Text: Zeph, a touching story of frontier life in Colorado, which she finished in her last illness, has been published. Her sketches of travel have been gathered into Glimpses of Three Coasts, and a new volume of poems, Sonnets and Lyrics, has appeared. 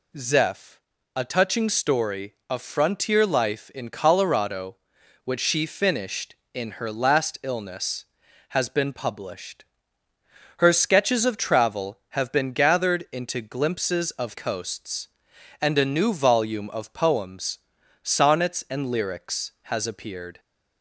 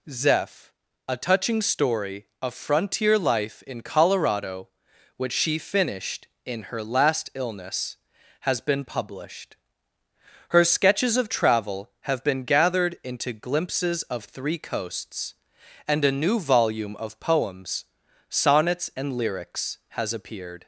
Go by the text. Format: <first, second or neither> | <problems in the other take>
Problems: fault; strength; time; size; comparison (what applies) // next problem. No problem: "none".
second | skips "Three"; at 14.3 s